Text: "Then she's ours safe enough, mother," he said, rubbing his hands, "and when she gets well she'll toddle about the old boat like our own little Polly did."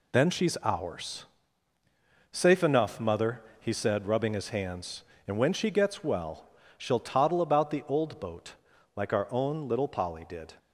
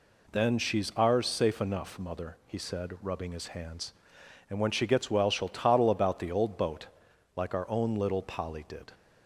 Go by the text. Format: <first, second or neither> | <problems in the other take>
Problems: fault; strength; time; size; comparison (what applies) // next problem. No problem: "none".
second | gets quieter; throughout; 6.5 dB // pauses between "ours" and "safe"; at 1.2 s; 1.0 s long // pauses between "well" and "she'll"; slight; at 6.4 s; 0.28 s long // pauses between "boat" and "like"; at 8.5 s; 0.42 s long; noticeable in the second